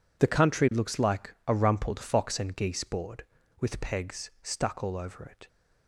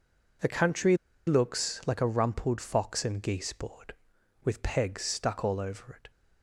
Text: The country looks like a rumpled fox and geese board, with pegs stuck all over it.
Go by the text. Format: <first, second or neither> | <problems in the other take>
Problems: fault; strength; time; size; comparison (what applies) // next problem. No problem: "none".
first | pauses between "country" and "looks"; slight; at 0.9 s; 0.30 s long